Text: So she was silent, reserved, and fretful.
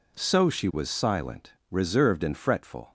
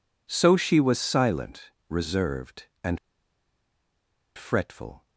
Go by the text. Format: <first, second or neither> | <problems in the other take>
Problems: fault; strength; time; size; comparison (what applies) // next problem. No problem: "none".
first | pauses between "and" and "fretful"; strong; at 2.9 s; 1.3 s long